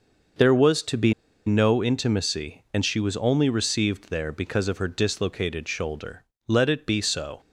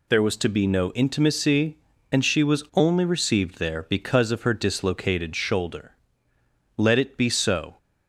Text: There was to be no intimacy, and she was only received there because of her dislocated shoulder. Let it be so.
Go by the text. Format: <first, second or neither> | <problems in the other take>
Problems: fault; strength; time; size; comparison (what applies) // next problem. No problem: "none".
second | pauses between "be" and "no"; slight; at 1.1 s; 0.34 s long